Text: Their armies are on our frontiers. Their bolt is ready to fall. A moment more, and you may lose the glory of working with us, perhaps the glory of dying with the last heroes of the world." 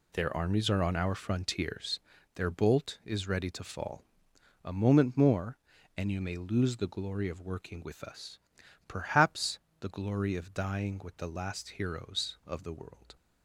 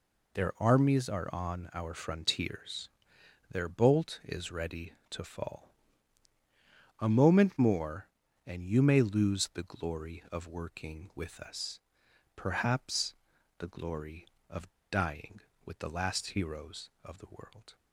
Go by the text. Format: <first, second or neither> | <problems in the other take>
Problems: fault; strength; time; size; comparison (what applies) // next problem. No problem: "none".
first | pauses between "perhaps" and "the"; at 13.1 s; 0.44 s long; slight in the first // pauses between "of" and "dying"; slight; at 14.6 s; 0.21 s long